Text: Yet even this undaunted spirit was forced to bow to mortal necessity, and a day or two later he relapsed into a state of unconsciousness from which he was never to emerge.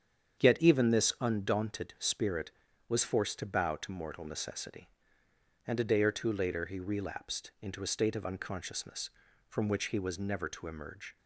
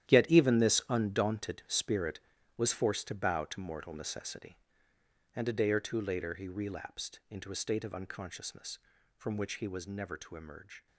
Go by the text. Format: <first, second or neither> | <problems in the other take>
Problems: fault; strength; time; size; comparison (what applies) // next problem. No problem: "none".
first | gets quieter; strong; throughout; 13 dB // starts louder than the rest; strong; until 1.1 s; 11.5 dB; strong in the first